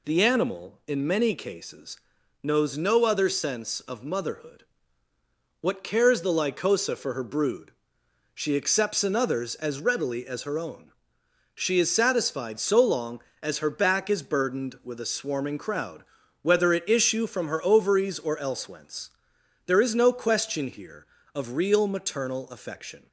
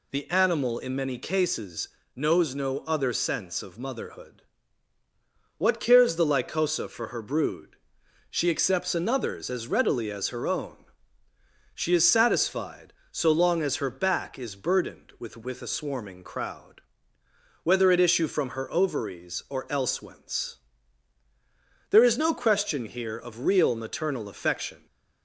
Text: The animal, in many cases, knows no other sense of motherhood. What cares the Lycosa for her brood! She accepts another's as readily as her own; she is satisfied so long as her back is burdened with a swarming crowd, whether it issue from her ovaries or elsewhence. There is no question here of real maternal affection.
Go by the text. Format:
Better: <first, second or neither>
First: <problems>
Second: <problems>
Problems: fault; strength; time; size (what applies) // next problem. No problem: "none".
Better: first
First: none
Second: says "with" twice; at 15.3 s